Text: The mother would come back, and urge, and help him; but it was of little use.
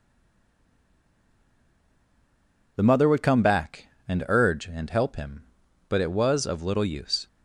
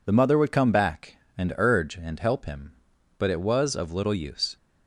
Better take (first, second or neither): second